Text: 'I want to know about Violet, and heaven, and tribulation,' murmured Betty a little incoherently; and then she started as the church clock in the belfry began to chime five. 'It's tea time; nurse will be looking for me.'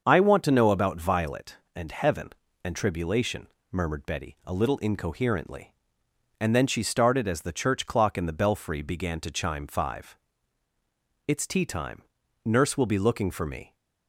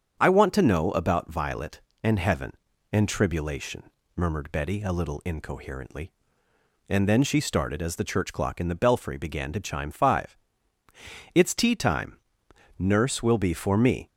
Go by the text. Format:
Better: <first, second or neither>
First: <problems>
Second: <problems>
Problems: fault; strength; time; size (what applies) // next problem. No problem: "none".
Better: first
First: starts louder than the rest; until 1.0 s; 6.5 dB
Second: starts louder than the rest; strong; until 1.2 s; 8 dB // skips "looking"; at 13.5 s